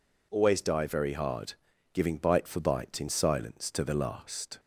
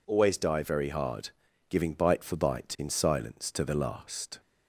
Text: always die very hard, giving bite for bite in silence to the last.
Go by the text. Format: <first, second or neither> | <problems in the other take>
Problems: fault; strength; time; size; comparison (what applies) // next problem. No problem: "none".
neither | none